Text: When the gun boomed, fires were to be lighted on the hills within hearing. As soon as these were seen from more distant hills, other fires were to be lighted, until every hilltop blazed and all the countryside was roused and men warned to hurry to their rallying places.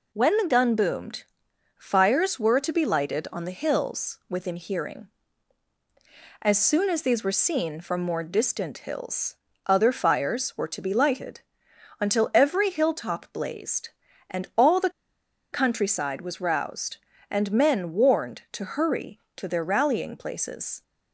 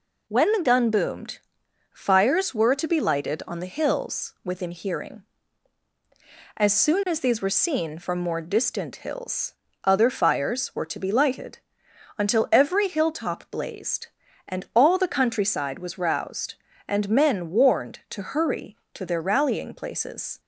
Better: second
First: pauses between "the" and "countryside"; noticeable; at 14.9 s; 0.62 s long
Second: none

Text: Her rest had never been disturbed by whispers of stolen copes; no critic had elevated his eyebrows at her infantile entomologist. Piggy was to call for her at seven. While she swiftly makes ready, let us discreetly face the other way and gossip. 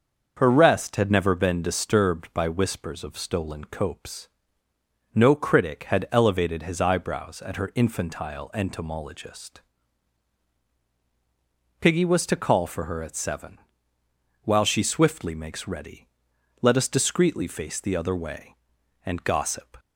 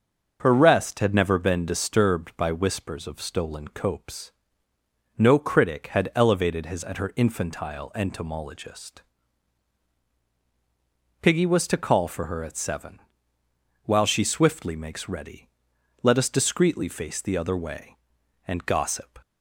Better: first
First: starts louder than the rest; until 1.3 s; 6.5 dB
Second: starts louder than the rest; until 1.4 s; 6.5 dB // skips "eyebrows"; at 6.8 s

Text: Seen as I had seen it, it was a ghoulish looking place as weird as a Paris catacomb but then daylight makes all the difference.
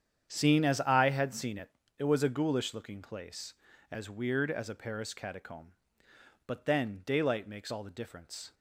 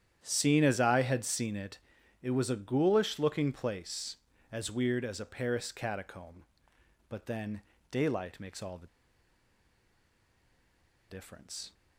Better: first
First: starts louder than the rest; strong; until 1.3 s; 8.5 dB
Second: starts louder than the rest; strong; until 1.2 s; 10 dB // pauses between "then" and "daylight"; slight; at 7.6 s; 0.30 s long // pauses between "the" and "difference"; strong; at 8.8 s; 2.2 s long

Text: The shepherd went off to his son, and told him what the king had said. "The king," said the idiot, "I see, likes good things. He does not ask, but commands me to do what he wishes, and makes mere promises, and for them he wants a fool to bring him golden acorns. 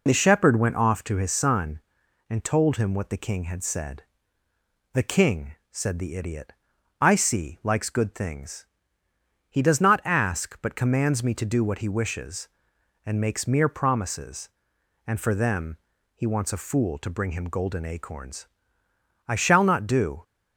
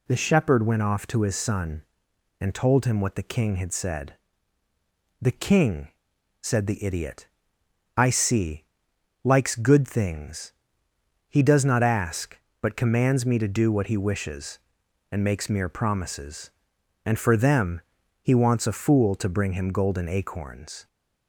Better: second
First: pauses between "them" and "he"; slight; at 15.7 s; 0.36 s long // goes on to say "I shall not do"; noticeable; from 19.2 s on; 0.96 s long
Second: pauses between "them" and "he"; at 17.8 s; 0.40 s long

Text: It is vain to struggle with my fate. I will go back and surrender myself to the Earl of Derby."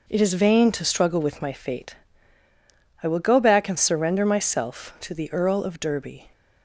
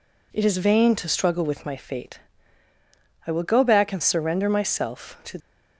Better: first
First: none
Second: stops before "the Earl of Derby"; at 5.4 s

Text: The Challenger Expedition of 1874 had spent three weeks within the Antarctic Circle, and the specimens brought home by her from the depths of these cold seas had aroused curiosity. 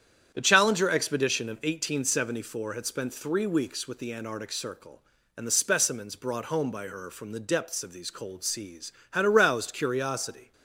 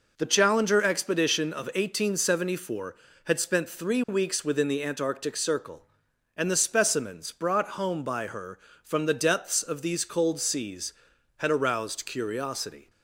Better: second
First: starts louder than the rest; strong; until 1.3 s; 9 dB // says "with" for "within"; at 3.8 s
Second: none

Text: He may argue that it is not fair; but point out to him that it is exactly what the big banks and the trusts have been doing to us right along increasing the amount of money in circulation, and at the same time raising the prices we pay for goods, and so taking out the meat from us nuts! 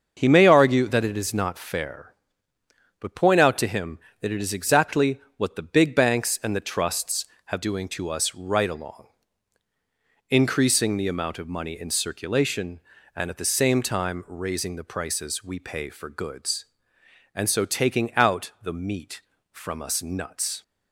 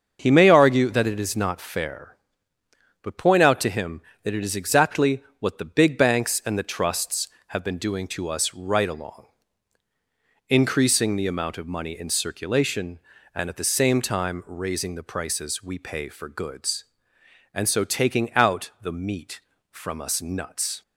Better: second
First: starts louder than the rest; until 1.1 s; 6.5 dB // pauses between "exactly" and "what"; slight; at 5.1 s; 0.16 s long // skips "been"; at 7.6 s // pauses between "along" and "increasing"; at 9.0 s; 1.2 s long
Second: starts louder than the rest; until 1.2 s; 6.5 dB // pauses between "exactly" and "what"; slight; at 5.2 s; 0.16 s long // pauses between "along" and "increasing"; at 9.2 s; 1.2 s long

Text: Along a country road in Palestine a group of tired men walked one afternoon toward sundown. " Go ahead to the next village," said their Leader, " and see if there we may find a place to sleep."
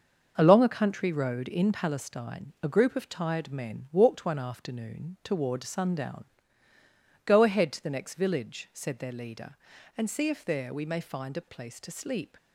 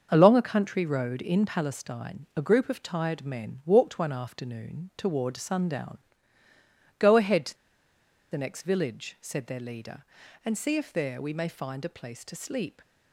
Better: first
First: starts louder than the rest; until 1.3 s; 6.5 dB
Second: starts louder than the rest; until 1.1 s; 6.5 dB // pauses between "to" and "the"; noticeable; at 7.5 s; 0.74 s long

